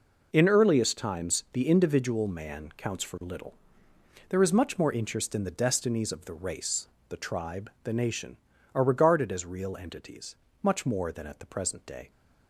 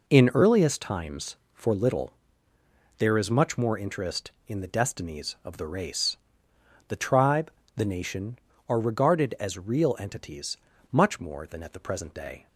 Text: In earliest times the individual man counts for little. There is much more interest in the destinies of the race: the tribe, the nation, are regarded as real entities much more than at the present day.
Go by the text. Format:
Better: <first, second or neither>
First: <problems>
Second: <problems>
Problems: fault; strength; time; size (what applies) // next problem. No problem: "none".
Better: first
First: pauses between "entities" and "much"; slight; at 10.3 s; 0.26 s long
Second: skips "the individual man counts"; at 1.4 s // pauses between "entities" and "much"; slight; at 10.5 s; 0.32 s long